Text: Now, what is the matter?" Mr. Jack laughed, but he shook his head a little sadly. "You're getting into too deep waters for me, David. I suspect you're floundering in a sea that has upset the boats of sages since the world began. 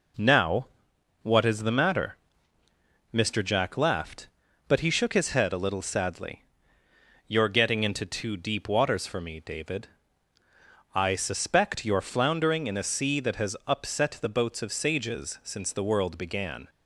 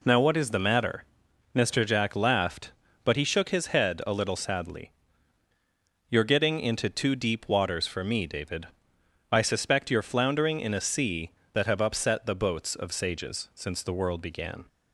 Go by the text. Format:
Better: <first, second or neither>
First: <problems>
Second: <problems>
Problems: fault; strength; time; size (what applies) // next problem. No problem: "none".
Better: first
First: none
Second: says "have" for "has"; at 11.6 s